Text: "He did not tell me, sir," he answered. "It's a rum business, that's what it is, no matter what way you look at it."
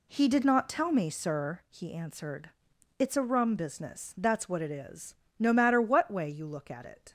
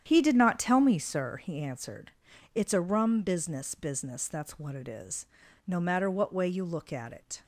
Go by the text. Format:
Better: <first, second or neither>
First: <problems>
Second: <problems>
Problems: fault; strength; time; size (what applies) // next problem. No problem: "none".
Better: first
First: none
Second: starts louder than the rest; strong; until 1.0 s; 9.5 dB // says "business" twice; at 3.7 s